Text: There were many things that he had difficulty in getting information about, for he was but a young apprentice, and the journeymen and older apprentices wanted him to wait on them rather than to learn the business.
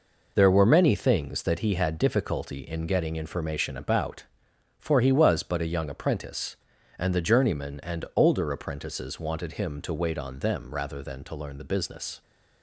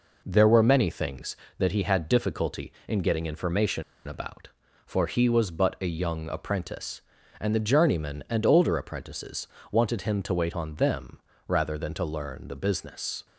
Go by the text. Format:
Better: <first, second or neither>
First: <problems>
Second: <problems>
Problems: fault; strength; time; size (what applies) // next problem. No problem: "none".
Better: first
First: none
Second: pauses between "information" and "about"; slight; at 3.8 s; 0.24 s long // pauses between "apprentices" and "wanted"; slight; at 9.4 s; 0.24 s long // pauses between "them" and "rather"; slight; at 11.1 s; 0.28 s long